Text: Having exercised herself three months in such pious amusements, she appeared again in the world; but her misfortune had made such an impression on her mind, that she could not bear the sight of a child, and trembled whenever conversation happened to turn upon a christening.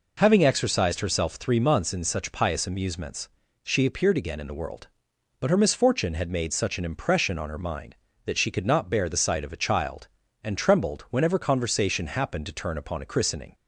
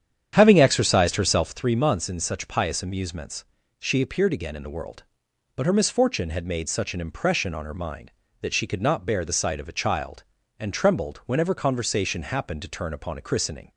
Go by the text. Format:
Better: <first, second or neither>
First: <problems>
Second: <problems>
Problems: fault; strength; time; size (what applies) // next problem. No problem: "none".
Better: first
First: none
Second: starts louder than the rest; strong; until 1.6 s; 9 dB